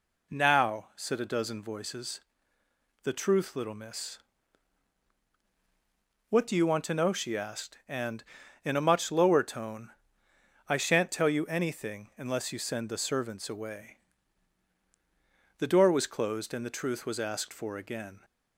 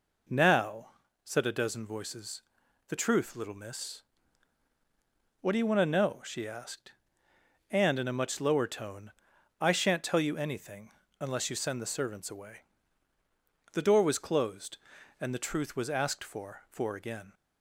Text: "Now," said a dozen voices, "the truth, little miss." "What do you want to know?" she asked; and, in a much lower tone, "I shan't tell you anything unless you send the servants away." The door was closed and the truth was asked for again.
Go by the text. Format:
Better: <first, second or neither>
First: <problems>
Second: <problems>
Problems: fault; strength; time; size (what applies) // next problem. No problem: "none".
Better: first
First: none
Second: pauses between "anything" and "unless"; slight; at 10.8 s; 0.30 s long // says "for" twice; at 16.6 s